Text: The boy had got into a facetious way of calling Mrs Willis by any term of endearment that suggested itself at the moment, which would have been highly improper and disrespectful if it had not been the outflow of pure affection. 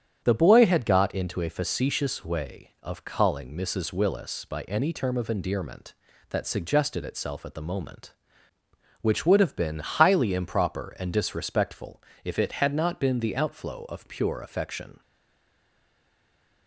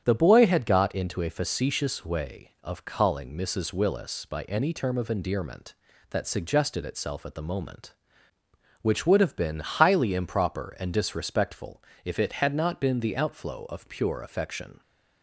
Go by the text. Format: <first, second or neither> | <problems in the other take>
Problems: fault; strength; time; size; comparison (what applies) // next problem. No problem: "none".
second | starts louder than the rest; strong; until 1.2 s; 8.5 dB; strong in the second // pauses between "disrespectful" and "if"; slight; at 12.0 s; 0.22 s long; slight in the second // stays silent after the last word; noticeable; from 15.0 s on; 1.6 s long